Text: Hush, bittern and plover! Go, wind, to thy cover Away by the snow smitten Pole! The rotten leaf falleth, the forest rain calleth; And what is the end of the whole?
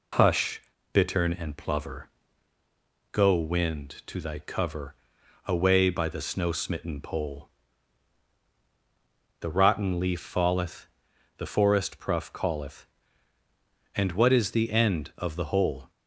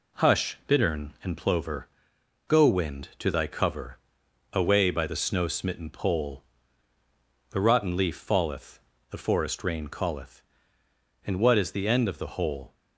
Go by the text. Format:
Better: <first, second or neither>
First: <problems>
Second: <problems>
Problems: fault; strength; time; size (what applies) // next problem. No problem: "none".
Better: second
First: pauses between "cover" and "Away"; noticeable; at 4.9 s; 0.54 s long // says "pruff" for "rain"; at 11.9 s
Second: pauses between "cover" and "Away"; noticeable; at 3.9 s; 0.54 s long